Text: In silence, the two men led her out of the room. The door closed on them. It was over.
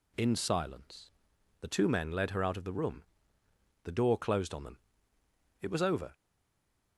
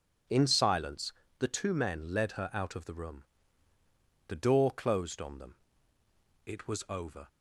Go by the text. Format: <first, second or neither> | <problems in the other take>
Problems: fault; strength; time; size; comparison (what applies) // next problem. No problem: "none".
second | stays silent after the last word; slight; from 6.1 s on; 0.8 s long